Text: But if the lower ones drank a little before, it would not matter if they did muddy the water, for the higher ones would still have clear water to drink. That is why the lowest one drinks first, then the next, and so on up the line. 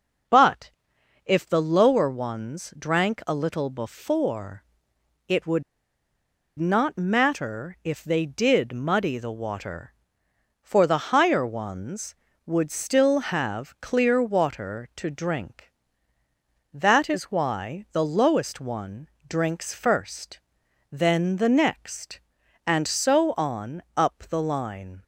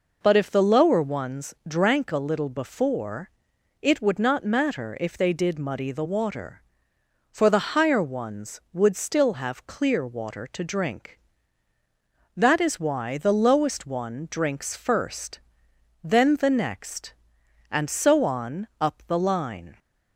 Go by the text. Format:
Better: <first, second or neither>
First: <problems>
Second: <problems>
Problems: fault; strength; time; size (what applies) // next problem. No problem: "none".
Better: second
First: pauses between "But" and "if"; noticeable; at 0.7 s; 0.54 s long // pauses between "would" and "not"; noticeable; at 5.6 s; 0.96 s long // pauses between "one" and "drinks"; slight; at 19.0 s; 0.20 s long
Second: none